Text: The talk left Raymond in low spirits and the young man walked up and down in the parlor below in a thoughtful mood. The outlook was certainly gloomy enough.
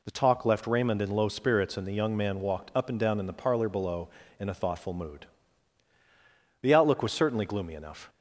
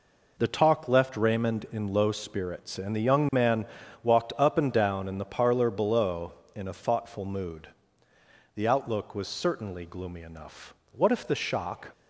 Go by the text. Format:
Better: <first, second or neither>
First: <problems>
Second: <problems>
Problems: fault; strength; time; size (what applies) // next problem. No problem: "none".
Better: first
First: none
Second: pauses between "man" and "walked"; slight; at 3.6 s; 0.36 s long // goes on to say "What if the shock"; noticeable; from 10.8 s on; 1.0 s long